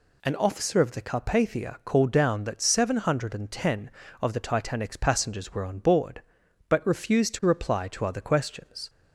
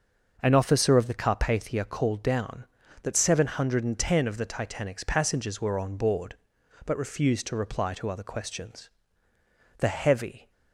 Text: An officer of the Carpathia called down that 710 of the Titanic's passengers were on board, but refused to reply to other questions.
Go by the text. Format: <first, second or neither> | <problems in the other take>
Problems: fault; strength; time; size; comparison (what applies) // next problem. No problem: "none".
first | starts louder than the rest; noticeable; until 1.4 s; 6 dB // goes on to say "The heavy"; noticeable; from 9.7 s on; 0.72 s long